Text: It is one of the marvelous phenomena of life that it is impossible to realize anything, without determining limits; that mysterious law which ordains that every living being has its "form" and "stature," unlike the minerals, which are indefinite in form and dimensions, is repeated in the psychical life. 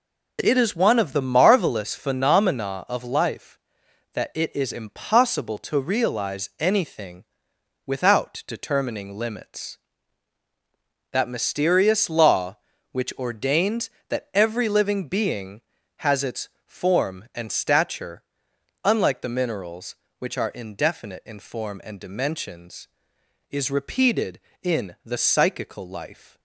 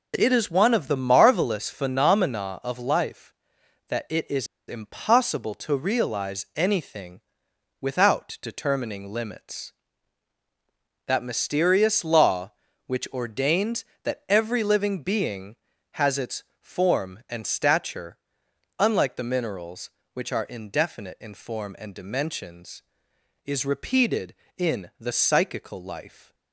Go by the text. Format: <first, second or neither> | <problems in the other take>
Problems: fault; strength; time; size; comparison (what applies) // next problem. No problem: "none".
first | pauses between "is" and "impossible"; slight; at 4.4 s; 0.21 s long // pauses between "its" and "form"; slight; at 16.4 s; 0.18 s long; slight in the first